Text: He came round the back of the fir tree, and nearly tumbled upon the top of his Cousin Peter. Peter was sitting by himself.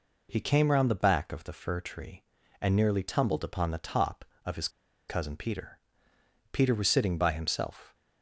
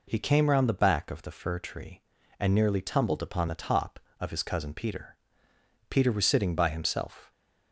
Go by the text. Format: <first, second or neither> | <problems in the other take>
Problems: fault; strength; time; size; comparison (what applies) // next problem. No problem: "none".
second | pauses between "his" and "Cousin"; at 4.6 s; 0.40 s long